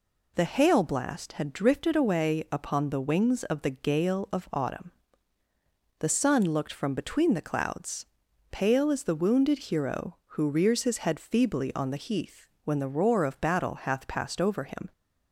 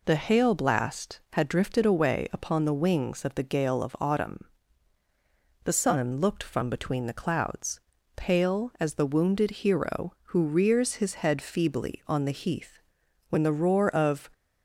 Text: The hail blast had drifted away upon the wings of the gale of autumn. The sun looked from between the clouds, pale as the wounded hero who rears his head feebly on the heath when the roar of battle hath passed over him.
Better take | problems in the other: first | pauses between "heath" and "when"; noticeable; at 12.7 s; 0.52 s long; slight in the first // stops before "battle hath passed over him"; at 14.3 s

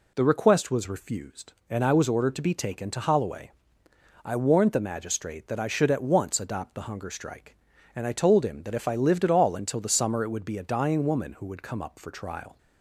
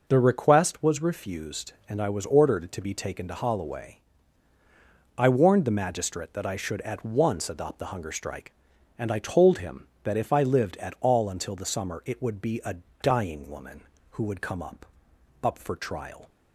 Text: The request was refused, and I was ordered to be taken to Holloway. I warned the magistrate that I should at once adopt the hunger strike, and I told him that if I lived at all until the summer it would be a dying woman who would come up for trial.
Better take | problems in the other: first | pauses between "a" and "dying"; slight; at 12.7 s; 0.26 s long // says "up" twice; at 15.4 s

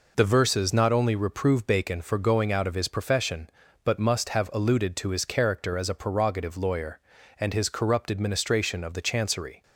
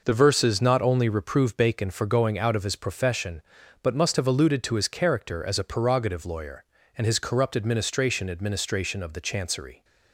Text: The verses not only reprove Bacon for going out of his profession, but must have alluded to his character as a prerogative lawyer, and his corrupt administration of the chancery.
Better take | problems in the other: first | says "administration" twice; at 8.3 s

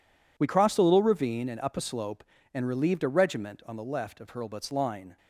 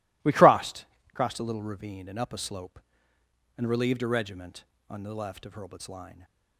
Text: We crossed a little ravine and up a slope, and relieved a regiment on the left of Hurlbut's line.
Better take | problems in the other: first | says "crossed" twice; at 1.1 s

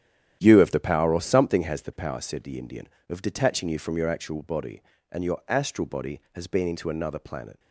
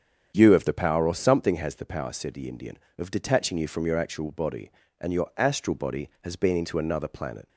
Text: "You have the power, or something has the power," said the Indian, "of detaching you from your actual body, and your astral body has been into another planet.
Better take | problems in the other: second | gets quieter; strong; throughout; 10.5 dB // starts louder than the rest; strong; until 1.4 s; 10.5 dB; strong in the second

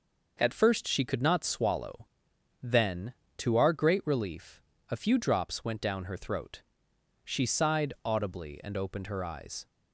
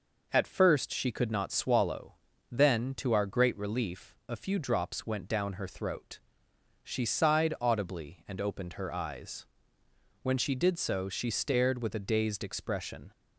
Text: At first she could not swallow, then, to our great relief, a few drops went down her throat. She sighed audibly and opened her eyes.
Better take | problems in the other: first | goes on to say "When she did so she stared with a dazed expression"; strong; from 10.2 s on; 2.9 s long

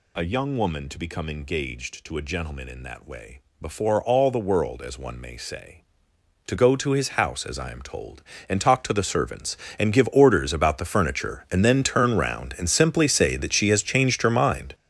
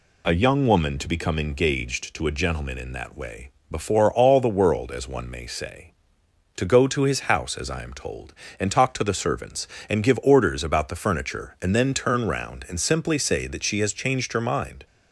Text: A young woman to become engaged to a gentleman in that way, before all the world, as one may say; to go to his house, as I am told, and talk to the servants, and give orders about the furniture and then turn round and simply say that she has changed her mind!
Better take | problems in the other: second | gets louder; strong; throughout; 11.5 dB

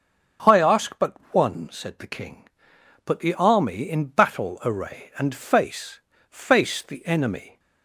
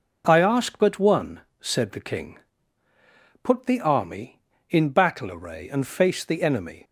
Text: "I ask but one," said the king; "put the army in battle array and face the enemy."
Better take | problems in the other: second | starts louder than the rest; strong; until 1.6 s; 7 dB // pauses between "but" and "one"; slight; at 1.1 s; 0.18 s long // says "face" twice; at 6.3 s

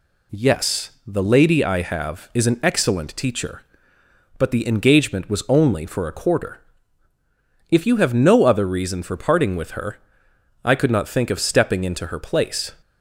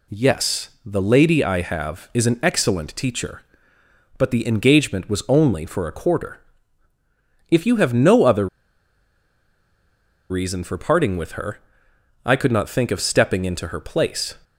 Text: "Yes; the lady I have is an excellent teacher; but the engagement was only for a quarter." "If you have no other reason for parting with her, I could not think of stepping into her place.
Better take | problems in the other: first | pauses between "other" and "reason"; strong; at 8.4 s; 1.8 s long

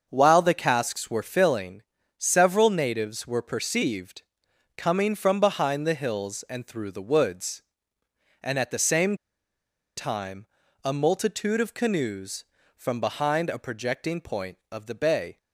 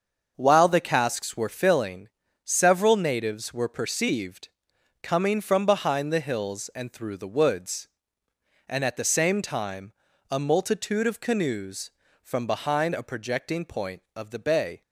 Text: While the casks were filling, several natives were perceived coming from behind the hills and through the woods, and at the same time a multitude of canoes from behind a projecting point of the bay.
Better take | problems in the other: second | starts louder than the rest; until 1.1 s; 6.5 dB; also in the second // pauses between "perceived" and "coming"; noticeable; at 4.2 s; 0.56 s long; noticeable in the second // pauses between "same" and "time"; noticeable; at 9.1 s; 0.80 s long // pauses between "time" and "a"; at 10.4 s; 0.38 s long; also in the second

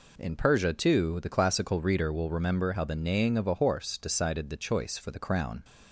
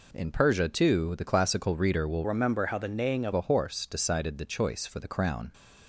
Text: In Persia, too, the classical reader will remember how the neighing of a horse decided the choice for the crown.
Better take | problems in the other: first | changes voice from "remember" to "of"; from 2.2 to 3.3 s; 1.1 s long

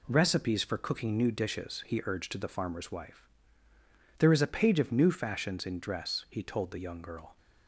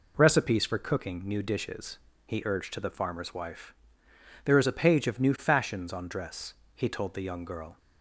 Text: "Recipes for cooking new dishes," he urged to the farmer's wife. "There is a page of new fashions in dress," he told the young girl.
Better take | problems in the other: first | says "on" for "in"; at 5.9 s

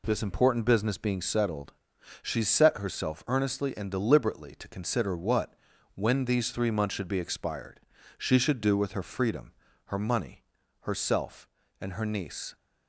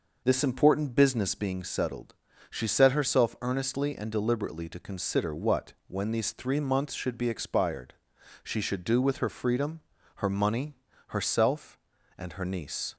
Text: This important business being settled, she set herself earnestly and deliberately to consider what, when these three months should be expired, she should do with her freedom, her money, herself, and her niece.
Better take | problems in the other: first | starts louder than the rest; noticeable; until 1.6 s; 5.5 dB

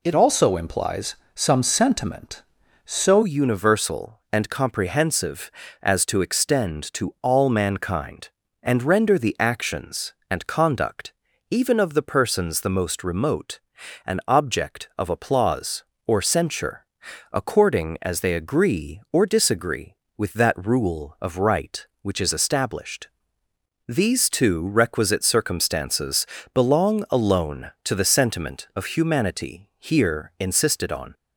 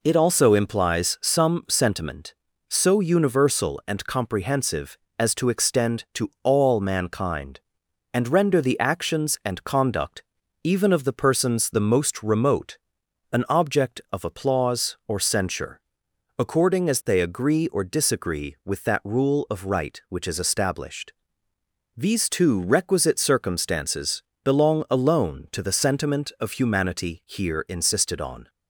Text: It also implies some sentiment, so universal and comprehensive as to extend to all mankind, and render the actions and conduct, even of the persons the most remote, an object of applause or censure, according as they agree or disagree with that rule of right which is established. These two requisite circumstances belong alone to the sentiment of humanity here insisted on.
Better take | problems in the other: second | changes voice from "also" to "so"; from 0.1 to 3.2 s; 3.1 s long // pauses between "implies" and "some"; slight; at 1.1 s; 0.20 s long // pauses between "circumstances" and "belong"; slight; at 26.2 s; 0.28 s long; slight in the second

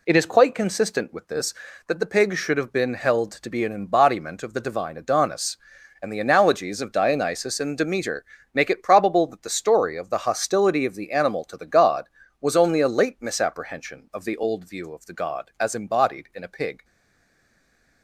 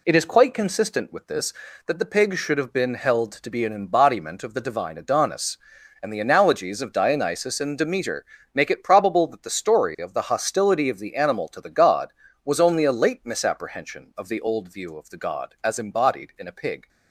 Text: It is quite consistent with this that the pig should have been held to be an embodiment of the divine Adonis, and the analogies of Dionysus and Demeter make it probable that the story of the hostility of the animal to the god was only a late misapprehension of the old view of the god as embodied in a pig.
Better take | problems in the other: second | pauses between "Demeter" and "make"; slight; at 8.2 s; 0.30 s long; slight in the second // stays silent after the last word; noticeable; from 16.8 s on; 1.2 s long

